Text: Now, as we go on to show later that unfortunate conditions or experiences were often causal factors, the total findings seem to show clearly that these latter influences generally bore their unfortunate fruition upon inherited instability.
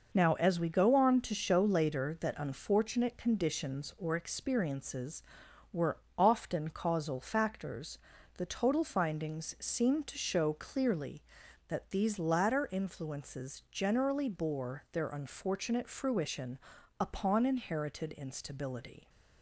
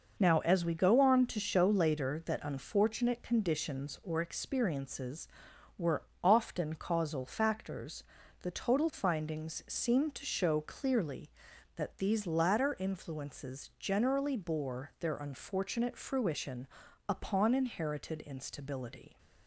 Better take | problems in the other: neither | pauses between "were" and "often"; slight; the same in both // pauses between "fruition" and "upon"; the same in both

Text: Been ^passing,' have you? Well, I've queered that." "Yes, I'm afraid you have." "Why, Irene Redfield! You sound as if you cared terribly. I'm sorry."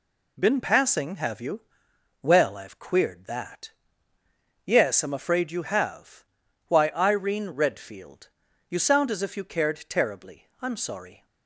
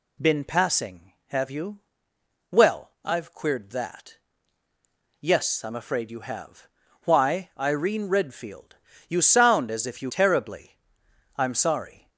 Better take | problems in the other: first | skips "cared"; at 10.0 s

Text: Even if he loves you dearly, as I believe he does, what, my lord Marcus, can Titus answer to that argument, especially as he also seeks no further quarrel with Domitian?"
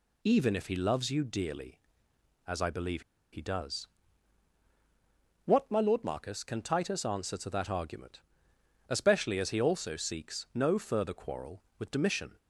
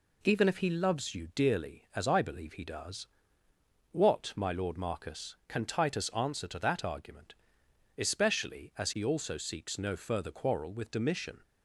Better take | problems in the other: second | pauses between "believe" and "he"; slight; at 3.0 s; 0.31 s long

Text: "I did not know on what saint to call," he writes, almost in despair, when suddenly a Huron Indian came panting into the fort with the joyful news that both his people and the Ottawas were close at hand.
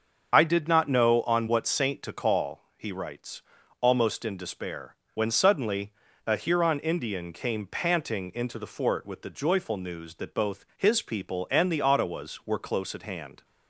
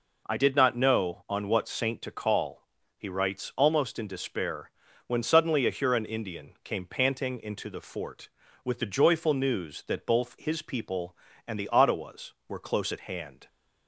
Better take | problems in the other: second | loses the start of "I"; at 0.3 s; 40 ms // starts louder than the rest; until 1.3 s; 6.5 dB // pauses between "suddenly" and "a"; slight; at 5.9 s; 0.34 s long

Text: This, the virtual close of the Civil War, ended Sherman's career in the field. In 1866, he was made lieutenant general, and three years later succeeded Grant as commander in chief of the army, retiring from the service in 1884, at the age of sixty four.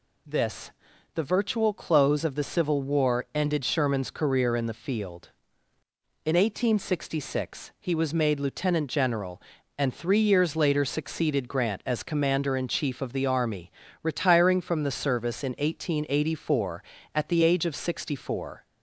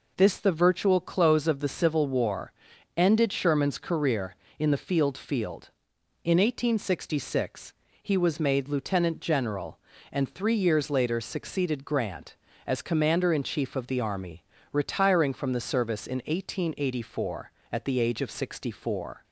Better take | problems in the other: first | says "field" twice; at 5.1 s

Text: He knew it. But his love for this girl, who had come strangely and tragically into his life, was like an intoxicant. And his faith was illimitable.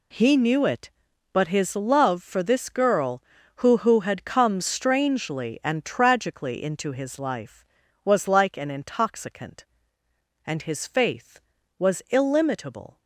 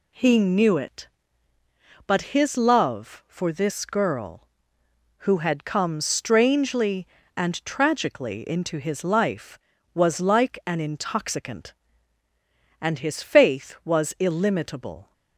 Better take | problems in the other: second | says "who" twice; at 3.7 s

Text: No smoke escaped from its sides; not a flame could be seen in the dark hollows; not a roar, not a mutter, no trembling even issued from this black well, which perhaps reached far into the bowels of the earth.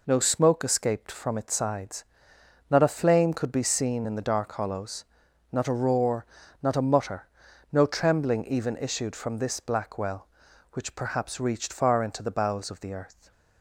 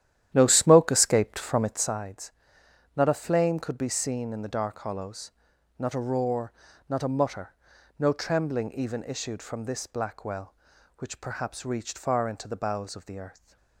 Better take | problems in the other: first | starts louder than the rest; strong; until 2.0 s; 11.5 dB

